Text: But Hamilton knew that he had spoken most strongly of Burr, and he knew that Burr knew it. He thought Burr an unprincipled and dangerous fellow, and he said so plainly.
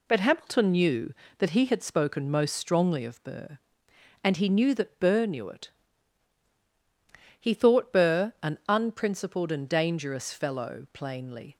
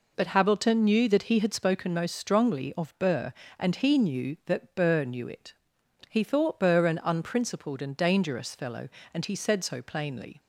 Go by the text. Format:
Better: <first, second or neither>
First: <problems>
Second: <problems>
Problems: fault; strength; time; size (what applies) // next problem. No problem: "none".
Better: second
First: skips "and he said so"; at 10.8 s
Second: none